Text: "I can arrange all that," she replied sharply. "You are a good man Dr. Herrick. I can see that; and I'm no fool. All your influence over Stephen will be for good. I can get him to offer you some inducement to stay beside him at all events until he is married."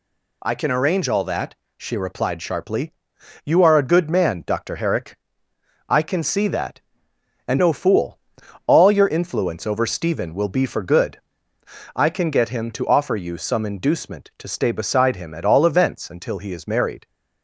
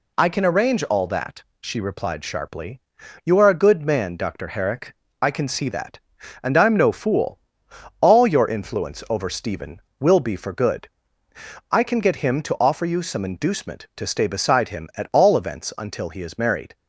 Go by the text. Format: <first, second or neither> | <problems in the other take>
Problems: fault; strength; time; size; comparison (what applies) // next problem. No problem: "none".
second | skips "I'm"; at 7.5 s